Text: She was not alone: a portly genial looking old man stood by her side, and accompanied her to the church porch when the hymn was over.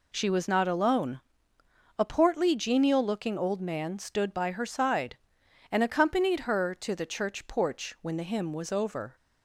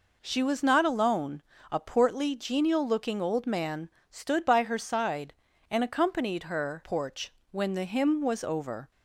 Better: first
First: none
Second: pauses between "man" and "stood"; slight; at 3.8 s; 0.22 s long // skips "to the church"; at 6.8 s // pauses between "porch" and "when"; slight; at 7.3 s; 0.18 s long

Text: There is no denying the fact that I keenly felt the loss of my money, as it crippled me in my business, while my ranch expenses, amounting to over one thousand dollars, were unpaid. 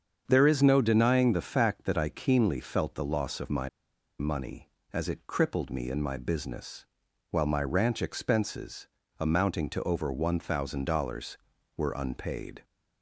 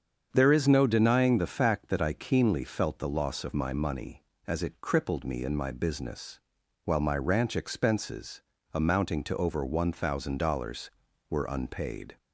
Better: second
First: starts louder than the rest; strong; until 1.2 s; 7.5 dB // pauses between "my" and "money"; noticeable; at 3.6 s; 0.49 s long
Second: starts louder than the rest; strong; until 1.3 s; 7.5 dB

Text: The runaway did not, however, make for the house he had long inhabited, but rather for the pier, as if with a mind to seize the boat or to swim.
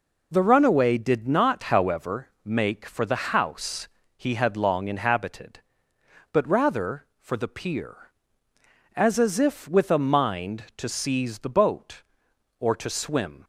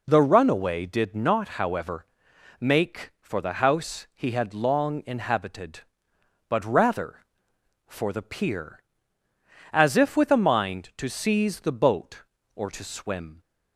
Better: second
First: pauses between "house" and "he"; slight; at 3.8 s; 0.30 s long // says "as" twice; at 9.1 s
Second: none

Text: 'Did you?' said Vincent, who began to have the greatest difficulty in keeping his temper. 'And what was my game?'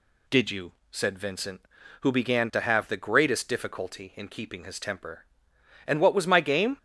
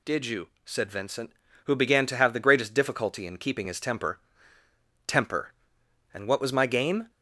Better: first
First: none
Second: says "temper" twice; at 5.0 s

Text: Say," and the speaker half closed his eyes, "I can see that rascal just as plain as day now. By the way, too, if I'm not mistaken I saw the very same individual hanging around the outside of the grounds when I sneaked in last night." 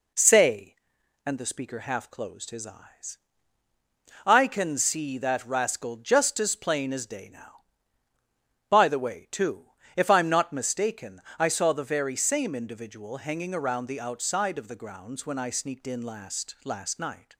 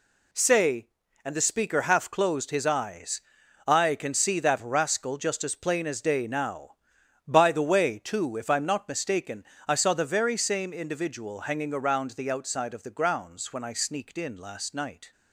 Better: second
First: pauses between "mistaken" and "I"; slight; at 11.2 s; 0.16 s long // says "last" twice; at 16.6 s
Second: pauses between "mistaken" and "I"; slight; at 9.4 s; 0.24 s long

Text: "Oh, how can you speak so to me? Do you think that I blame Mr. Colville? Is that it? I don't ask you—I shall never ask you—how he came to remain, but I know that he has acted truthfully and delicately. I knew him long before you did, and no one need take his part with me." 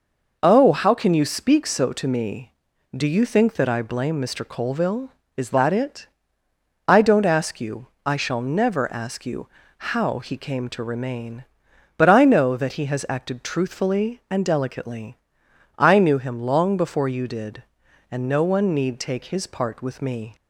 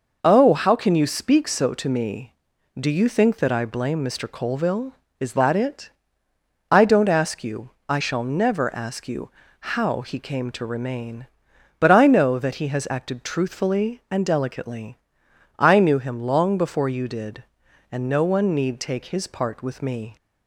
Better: neither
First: none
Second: none

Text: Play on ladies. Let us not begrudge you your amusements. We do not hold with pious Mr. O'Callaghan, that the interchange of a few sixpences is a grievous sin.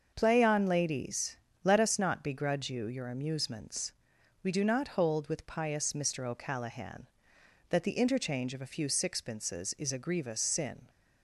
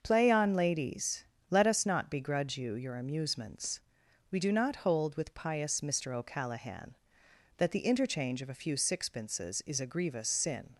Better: neither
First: starts louder than the rest; until 1.1 s; 6.5 dB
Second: starts louder than the rest; until 1.0 s; 6.5 dB

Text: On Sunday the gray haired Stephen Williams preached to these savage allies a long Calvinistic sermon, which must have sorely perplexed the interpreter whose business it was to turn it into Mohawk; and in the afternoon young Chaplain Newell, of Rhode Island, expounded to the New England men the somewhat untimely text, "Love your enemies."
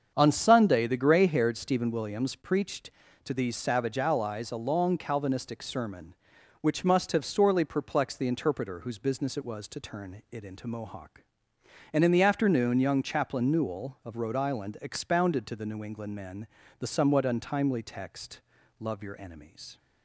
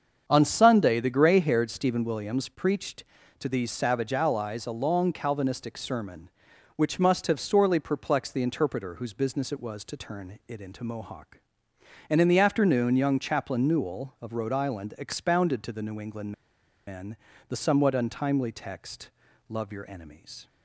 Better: first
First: starts louder than the rest; strong; until 1.1 s; 7 dB // pauses between "men" and "the"; slight; at 16.4 s; 0.32 s long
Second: starts louder than the rest; strong; until 1.2 s; 7 dB // pauses between "England" and "men"; noticeable; at 16.3 s; 0.54 s long // pauses between "men" and "the"; slight; at 17.1 s; 0.32 s long

